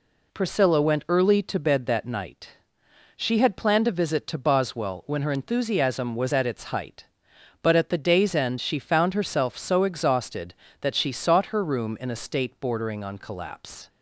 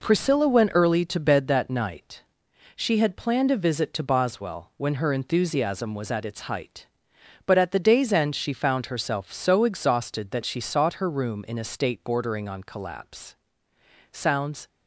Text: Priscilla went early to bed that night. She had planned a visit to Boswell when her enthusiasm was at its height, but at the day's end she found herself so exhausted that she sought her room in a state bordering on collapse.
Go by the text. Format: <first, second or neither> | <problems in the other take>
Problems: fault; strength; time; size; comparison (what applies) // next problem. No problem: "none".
first | goes on to say "Sounds"; from 14.1 s on; 0.56 s long